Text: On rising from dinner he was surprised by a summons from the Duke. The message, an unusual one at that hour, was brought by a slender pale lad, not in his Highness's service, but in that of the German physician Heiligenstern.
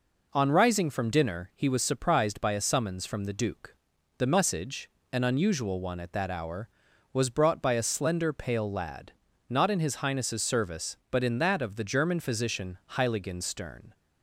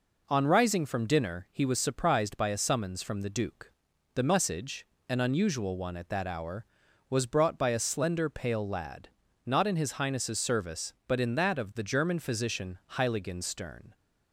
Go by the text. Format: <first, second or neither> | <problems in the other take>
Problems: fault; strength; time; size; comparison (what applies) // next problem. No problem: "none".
neither | pauses between "physician" and "Heiligenstern"; slight; the same in both